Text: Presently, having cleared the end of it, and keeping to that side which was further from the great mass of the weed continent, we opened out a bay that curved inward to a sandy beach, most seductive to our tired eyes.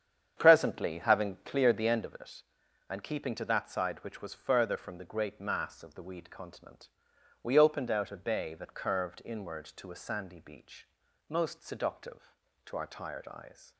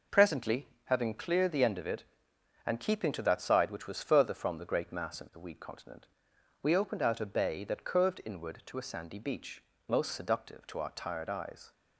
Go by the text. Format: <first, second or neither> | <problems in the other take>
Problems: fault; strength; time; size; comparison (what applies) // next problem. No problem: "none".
second | starts louder than the rest; strong; until 2.1 s; 8.5 dB